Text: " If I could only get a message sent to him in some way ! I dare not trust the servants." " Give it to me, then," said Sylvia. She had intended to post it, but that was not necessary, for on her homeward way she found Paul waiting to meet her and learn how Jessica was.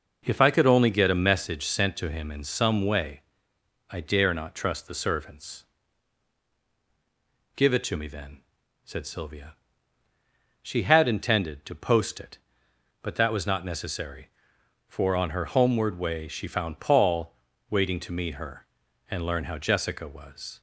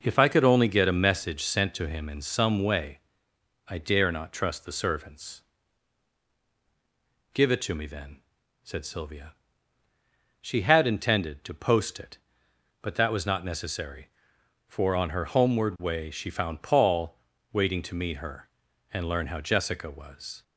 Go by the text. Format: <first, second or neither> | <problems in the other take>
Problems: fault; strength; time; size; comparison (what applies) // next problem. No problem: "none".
neither | pauses between "Paul" and "waiting"; slight; the same in both